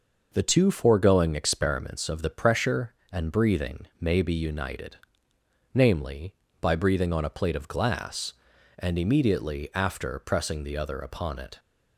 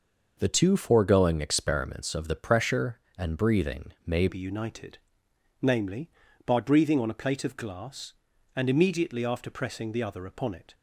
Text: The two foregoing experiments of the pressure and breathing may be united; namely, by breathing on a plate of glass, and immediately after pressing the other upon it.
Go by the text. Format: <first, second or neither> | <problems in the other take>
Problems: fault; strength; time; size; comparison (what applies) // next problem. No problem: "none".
first | pauses between "breathing" and "may"; slight; at 3.9 s; 0.16 s long; slight in the first // changes voice at "be"; from 4.2 s on; 6.5 s long